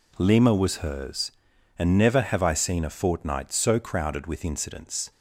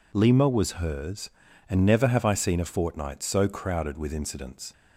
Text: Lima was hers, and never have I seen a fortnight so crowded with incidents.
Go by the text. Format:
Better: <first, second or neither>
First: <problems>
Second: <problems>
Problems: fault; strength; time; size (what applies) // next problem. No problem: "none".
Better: neither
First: none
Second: none